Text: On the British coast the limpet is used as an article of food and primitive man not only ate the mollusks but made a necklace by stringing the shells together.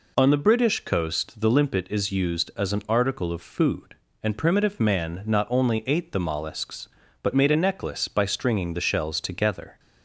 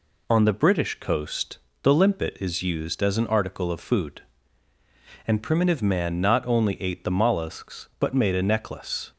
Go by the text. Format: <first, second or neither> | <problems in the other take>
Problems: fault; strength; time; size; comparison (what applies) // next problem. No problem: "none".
first | pauses between "coast" and "the"; slight; at 1.5 s; 0.24 s long // stops before "by stringing the shells together"; at 9.1 s